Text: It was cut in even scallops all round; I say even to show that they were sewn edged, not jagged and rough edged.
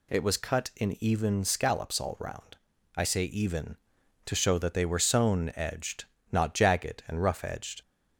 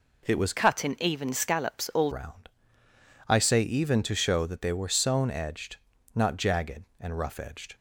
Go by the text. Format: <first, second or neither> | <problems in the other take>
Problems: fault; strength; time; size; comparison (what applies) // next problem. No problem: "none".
first | changes voice from "cut" to "all"; from 0.5 to 2.1 s; 1.6 s long